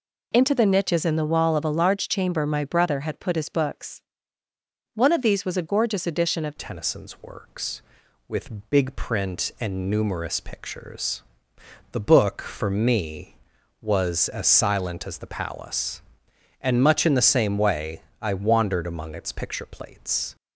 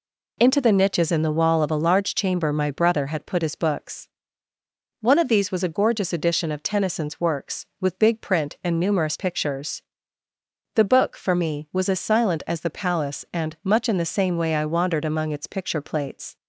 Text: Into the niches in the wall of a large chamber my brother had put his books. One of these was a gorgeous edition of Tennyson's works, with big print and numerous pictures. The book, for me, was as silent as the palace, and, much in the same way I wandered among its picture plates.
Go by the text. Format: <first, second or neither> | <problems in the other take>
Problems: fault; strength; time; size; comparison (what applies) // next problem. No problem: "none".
second | changes voice at "Tennyson's"; from 6.5 s on; 13.8 s long // pauses between "way" and "I"; slight; at 18.0 s; 0.20 s long